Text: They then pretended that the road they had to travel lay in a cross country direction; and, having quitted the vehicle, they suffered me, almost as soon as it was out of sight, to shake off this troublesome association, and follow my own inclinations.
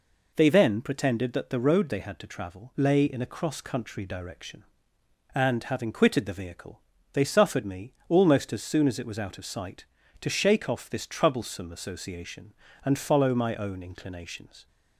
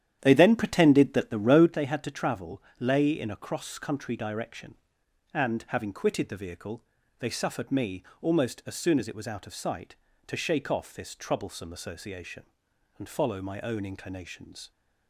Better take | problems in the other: first | starts louder than the rest; strong; until 1.7 s; 10.5 dB // pauses between "travel" and "lay"; slight; at 2.6 s; 0.18 s long

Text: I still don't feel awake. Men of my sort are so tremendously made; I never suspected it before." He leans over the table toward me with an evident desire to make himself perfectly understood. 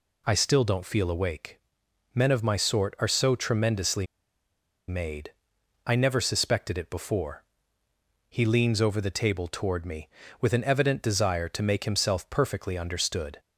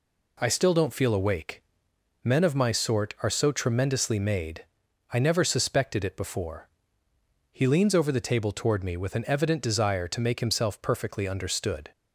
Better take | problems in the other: second | pauses between "tremendously" and "made"; noticeable; at 4.0 s; 0.83 s long

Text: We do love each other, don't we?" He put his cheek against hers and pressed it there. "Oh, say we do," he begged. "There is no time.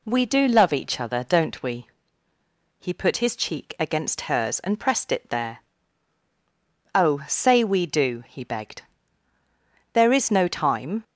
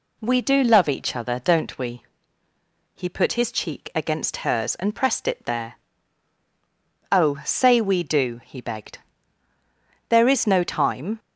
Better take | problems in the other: neither | none

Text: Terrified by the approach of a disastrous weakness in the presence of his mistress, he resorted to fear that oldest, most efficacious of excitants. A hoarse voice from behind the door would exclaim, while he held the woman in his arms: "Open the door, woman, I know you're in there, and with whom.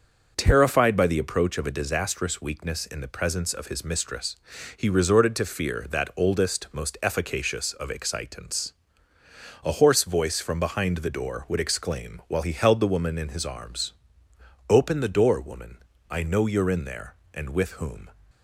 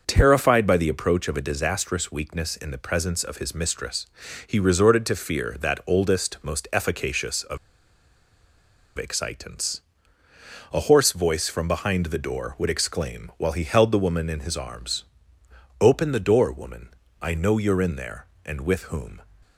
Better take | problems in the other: first | pauses between "of" and "excitants"; strong; at 7.5 s; 1.3 s long

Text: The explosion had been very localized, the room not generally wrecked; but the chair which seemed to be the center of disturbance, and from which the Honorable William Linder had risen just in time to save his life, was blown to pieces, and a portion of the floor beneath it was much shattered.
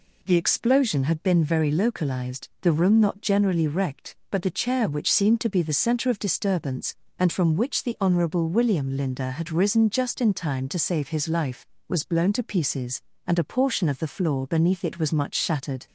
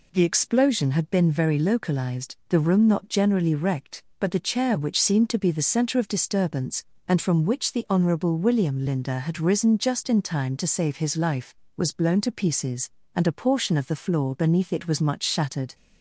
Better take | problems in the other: neither | none

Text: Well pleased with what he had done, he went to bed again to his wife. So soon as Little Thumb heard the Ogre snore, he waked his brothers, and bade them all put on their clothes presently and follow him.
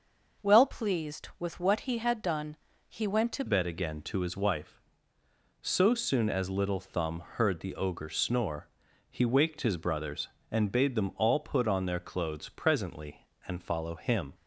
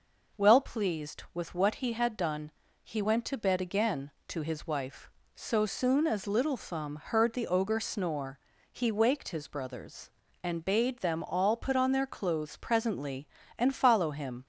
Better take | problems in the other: second | changes voice at "bed"; from 3.4 s on; 10.9 s long

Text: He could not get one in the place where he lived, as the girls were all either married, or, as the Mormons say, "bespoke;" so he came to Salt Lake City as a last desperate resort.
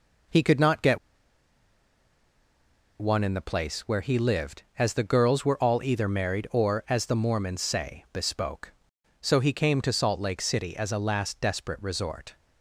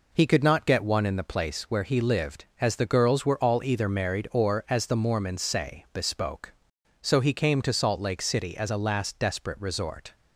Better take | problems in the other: second | pauses between "get" and "one"; strong; at 0.9 s; 2.0 s long

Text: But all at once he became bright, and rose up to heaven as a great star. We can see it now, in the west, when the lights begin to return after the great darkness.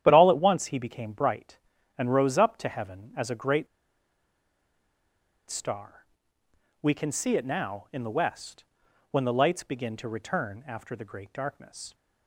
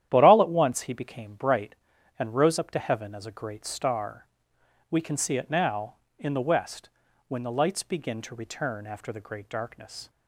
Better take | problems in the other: second | starts louder than the rest; strong; until 1.0 s; 10.5 dB; strong in the second // pauses between "great" and "star"; strong; at 3.6 s; 1.8 s long

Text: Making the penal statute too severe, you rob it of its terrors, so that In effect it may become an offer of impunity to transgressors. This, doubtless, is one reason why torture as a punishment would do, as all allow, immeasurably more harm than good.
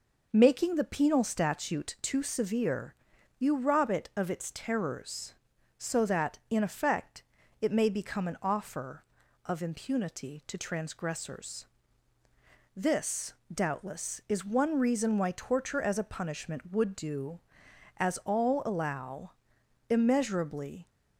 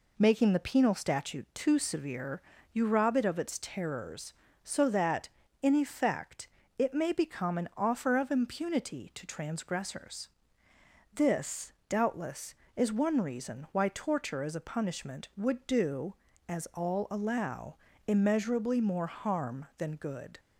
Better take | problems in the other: second | pauses between "effect" and "it"; slight; at 7.2 s; 0.36 s long; slight in the second // stops before "more harm than good"; at 20.8 s

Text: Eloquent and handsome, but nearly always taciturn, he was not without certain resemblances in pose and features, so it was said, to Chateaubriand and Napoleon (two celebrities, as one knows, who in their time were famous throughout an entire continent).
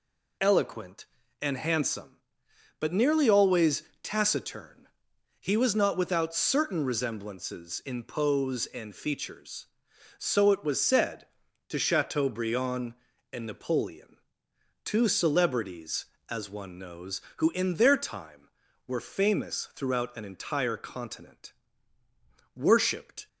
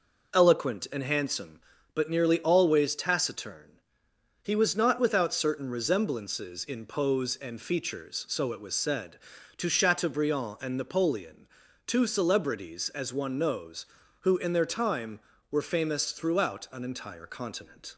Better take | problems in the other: second | pauses between "always" and "taciturn"; slight; at 3.8 s; 0.18 s long // goes on to say "Worshipped"; noticeable; from 22.5 s on; 0.72 s long

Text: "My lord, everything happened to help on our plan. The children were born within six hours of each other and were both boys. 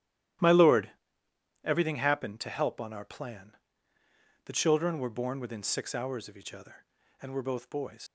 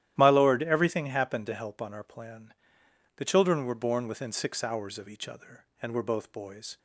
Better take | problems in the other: second | starts louder than the rest; strong; until 2.1 s; 13 dB; strong in the second // leaves "boys" unfinished; at 8.0 s; 85 ms

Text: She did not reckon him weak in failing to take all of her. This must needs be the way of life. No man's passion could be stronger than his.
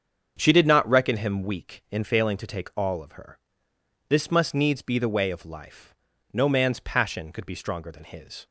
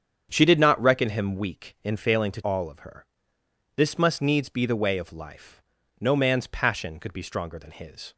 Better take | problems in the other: first | starts louder than the rest; strong; until 1.3 s; 8 dB; strong in the first // skips "take"; at 2.4 s

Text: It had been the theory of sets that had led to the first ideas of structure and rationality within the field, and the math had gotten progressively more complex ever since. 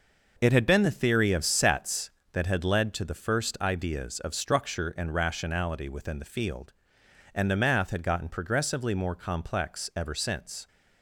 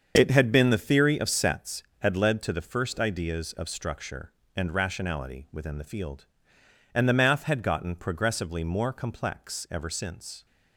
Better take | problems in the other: first | starts louder than the rest; until 1.1 s; 7 dB // skips "that"; at 1.9 s

